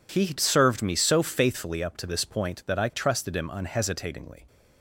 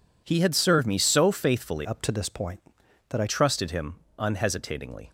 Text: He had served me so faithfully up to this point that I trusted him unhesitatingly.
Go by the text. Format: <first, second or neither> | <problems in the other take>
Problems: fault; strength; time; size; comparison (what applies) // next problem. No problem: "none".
first | changes voice from "up" to "I"; from 1.8 to 3.2 s; 1.4 s long // pauses between "him" and "unhesitatingly"; slight; at 3.9 s; 0.20 s long